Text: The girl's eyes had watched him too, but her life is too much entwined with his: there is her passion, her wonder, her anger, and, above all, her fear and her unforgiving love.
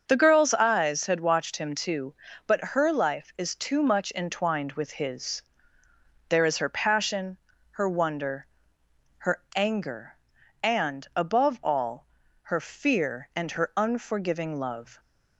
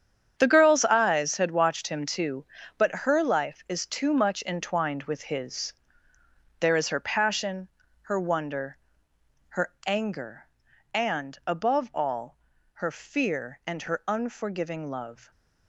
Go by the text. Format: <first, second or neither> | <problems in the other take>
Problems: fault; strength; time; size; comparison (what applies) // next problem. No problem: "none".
first | gets quieter; strong; throughout; 12.5 dB // starts louder than the rest; strong; until 1.3 s; 8.5 dB; also in the first